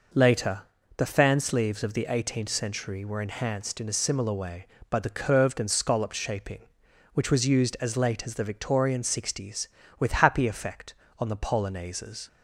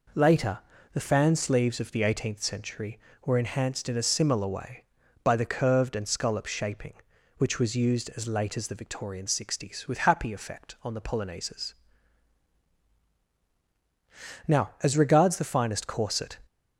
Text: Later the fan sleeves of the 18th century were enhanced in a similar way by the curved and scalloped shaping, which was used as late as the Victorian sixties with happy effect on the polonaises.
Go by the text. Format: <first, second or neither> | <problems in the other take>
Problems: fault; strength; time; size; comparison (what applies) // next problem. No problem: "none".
first | pauses between "Later" and "the"; slight; at 0.5 s; 0.34 s long; slight in the first // goes on to say "Now as regards the finest corset"; strong; from 14.4 s on; 1.9 s long